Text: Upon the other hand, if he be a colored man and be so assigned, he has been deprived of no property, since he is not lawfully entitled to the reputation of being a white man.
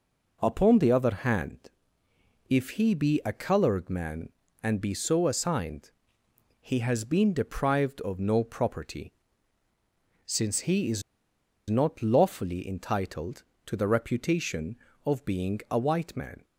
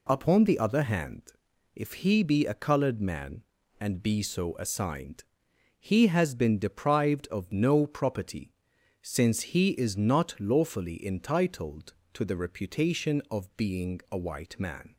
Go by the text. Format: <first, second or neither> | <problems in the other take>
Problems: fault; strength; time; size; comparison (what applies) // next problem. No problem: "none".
second | pauses between "is" and "not"; noticeable; at 11.0 s; 0.68 s long